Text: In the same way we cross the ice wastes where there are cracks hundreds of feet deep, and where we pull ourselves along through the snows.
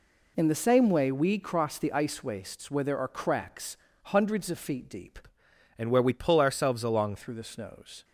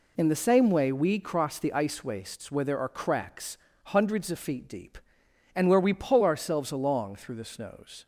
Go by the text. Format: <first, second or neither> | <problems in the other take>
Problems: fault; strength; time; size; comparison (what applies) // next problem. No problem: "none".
second | pauses between "cracks" and "hundreds"; slight; at 3.7 s; 0.26 s long; slight in the second // changes voice from "and" to "along"; from 5.7 to 7.1 s; 1.4 s long